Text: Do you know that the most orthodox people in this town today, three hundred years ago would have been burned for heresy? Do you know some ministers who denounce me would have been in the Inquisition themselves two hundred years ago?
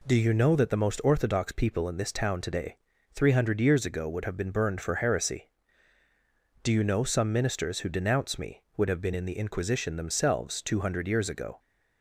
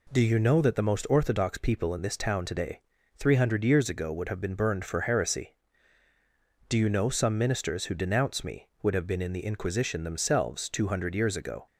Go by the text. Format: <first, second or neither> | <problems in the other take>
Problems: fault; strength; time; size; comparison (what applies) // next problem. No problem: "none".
neither | none